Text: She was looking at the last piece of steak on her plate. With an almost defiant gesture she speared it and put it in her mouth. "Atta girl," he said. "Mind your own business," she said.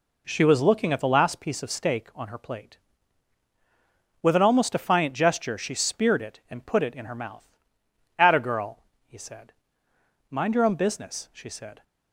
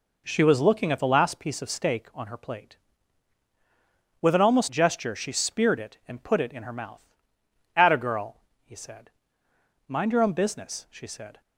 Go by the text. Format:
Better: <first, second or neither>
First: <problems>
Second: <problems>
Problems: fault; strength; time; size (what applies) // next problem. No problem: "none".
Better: first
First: none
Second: skips "defiant"; at 4.7 s